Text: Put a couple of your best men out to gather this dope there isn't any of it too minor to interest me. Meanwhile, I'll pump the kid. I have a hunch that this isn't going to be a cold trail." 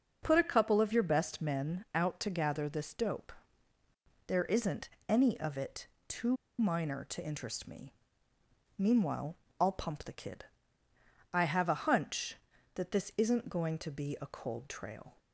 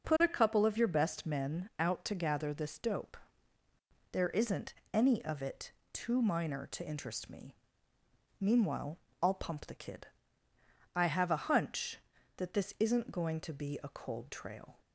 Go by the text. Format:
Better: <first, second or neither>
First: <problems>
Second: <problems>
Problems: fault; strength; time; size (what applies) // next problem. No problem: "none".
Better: second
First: starts louder than the rest; until 1.2 s; 6.5 dB // pauses between "dope" and "there"; noticeable; at 3.3 s; 0.92 s long // pauses between "isn't" and "any"; slight; at 4.8 s; 0.18 s long // pauses between "it" and "too"; slight; at 5.8 s; 0.22 s long // pauses between "too" and "minor"; slight; at 6.3 s; 0.24 s long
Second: pauses between "dope" and "there"; noticeable; at 3.1 s; 0.92 s long // pauses between "isn't" and "any"; slight; at 4.7 s; 0.18 s long // pauses between "it" and "too"; slight; at 5.7 s; 0.22 s long